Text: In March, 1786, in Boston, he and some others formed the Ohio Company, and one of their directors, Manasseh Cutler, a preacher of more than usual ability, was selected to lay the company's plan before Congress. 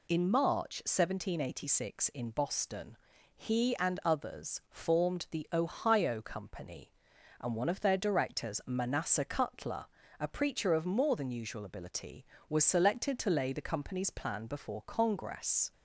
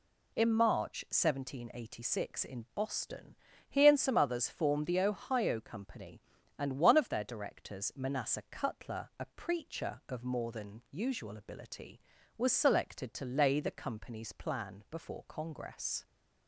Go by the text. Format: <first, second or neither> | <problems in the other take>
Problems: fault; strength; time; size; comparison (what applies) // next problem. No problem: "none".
second | skips "some"; at 4.0 s